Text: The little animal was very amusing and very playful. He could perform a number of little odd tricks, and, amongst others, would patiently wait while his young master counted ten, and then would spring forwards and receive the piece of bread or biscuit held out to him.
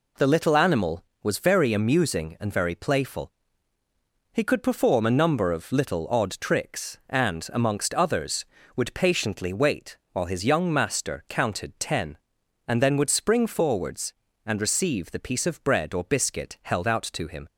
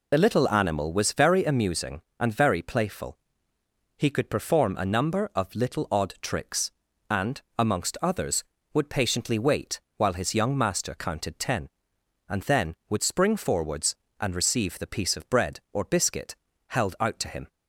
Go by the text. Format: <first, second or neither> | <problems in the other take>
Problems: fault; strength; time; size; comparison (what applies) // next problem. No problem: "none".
first | loses the start of "The"; at 0.1 s; 40 ms // pauses between "wait" and "while"; slight; at 9.8 s; 0.16 s long; slight in the first // pauses between "biscuit" and "held"; slight; at 16.3 s; 0.32 s long